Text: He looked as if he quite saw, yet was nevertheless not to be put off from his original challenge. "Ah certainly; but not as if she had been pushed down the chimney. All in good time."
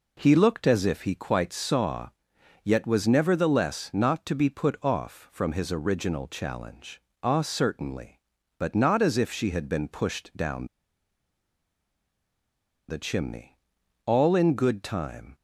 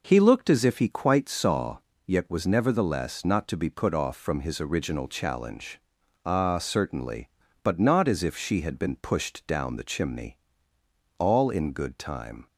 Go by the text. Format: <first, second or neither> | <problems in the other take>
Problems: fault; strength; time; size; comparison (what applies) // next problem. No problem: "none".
second | pauses between "down" and "the"; strong; at 10.6 s; 2.2 s long